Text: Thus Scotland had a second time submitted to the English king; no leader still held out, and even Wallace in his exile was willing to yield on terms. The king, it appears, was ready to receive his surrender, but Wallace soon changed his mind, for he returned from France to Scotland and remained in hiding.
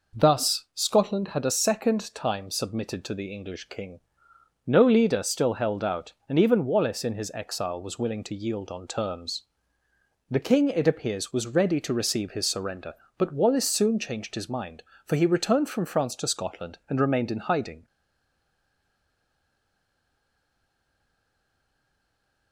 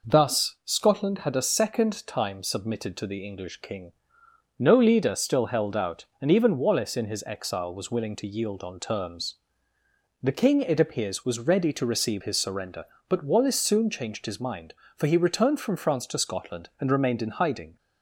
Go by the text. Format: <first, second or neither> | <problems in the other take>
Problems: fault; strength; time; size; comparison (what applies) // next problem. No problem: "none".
second | stays silent after the last word; strong; from 17.8 s on; 4.7 s long